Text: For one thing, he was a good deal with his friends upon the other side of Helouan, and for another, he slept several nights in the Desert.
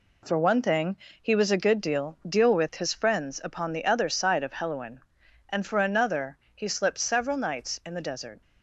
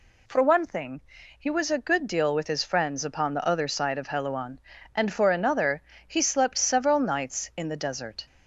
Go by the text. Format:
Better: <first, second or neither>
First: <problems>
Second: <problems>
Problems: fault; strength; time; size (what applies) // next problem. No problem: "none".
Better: second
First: says "deal" twice; at 2.2 s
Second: none